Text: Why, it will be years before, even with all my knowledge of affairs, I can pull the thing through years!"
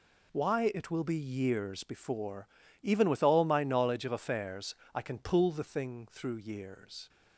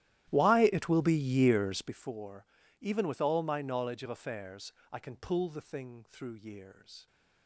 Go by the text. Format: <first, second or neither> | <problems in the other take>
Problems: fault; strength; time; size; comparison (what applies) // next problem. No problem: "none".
first | starts louder than the rest; strong; until 2.1 s; 13.5 dB